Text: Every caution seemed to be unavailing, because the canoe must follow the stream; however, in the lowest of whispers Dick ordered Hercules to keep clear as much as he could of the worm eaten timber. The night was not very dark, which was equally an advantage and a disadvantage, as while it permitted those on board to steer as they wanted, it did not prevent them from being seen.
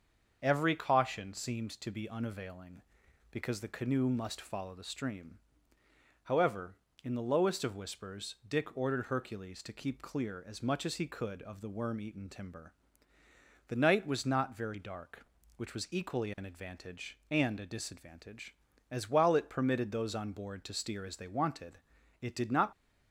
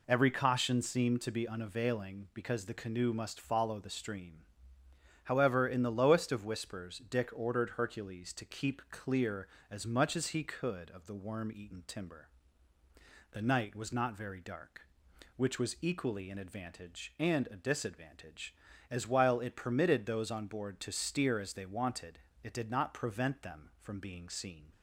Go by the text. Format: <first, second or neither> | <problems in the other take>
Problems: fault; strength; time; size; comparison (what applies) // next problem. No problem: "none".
second | starts louder than the rest; until 1.4 s; 6.5 dB // stops before "prevent them from being seen"; at 22.7 s